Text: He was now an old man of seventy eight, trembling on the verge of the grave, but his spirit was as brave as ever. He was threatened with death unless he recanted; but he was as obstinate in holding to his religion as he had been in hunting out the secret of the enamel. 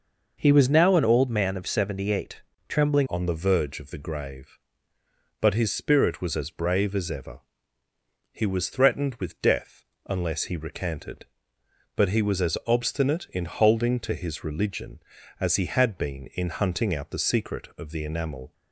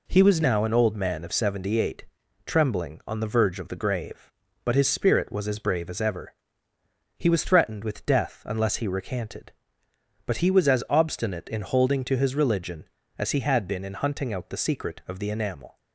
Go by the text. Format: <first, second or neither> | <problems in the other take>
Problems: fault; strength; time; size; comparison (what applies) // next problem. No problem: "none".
second | changes voice at "on"; from 3.0 s on; 15.5 s long // pauses between "death" and "unless"; slight; at 9.8 s; 0.24 s long